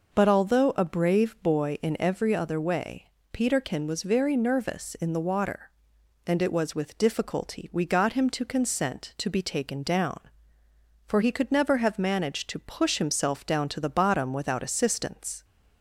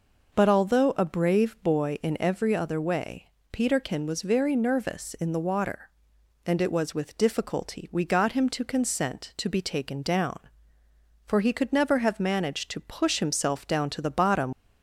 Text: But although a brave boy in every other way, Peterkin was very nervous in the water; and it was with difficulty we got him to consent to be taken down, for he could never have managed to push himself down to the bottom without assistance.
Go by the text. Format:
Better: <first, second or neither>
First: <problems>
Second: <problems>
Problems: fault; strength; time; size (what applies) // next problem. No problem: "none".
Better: first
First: none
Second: stops before "without assistance"; at 14.5 s